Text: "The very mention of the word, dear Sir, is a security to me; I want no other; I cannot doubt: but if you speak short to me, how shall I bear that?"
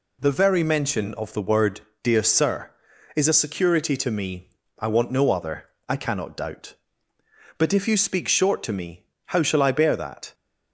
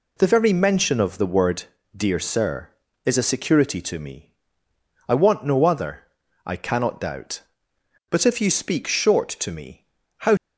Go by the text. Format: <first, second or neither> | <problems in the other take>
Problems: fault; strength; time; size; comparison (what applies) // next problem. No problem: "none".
first | stops before "shall I bear that"; at 10.3 s